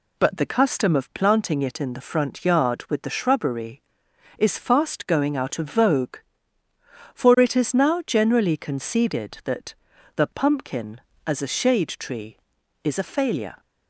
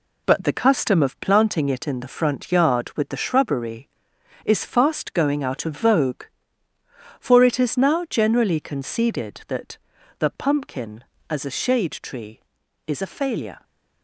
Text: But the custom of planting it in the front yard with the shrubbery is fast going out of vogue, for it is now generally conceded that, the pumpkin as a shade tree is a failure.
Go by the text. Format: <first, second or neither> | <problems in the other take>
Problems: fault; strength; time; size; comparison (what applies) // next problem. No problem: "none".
first | gets quieter; noticeable; throughout; 5.5 dB